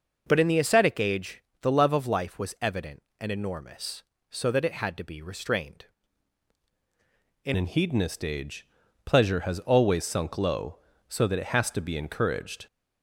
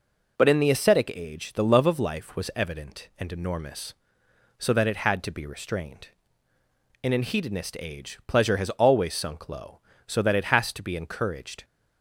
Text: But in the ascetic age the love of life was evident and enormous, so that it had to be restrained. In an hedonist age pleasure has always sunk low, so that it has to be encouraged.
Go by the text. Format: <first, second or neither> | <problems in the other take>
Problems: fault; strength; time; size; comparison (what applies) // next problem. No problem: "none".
second | pauses between "age" and "the"; slight; at 1.4 s; 0.20 s long // changes voice at "an"; from 7.5 s on; 5.1 s long // pauses between "age" and "pleasure"; at 8.6 s; 0.38 s long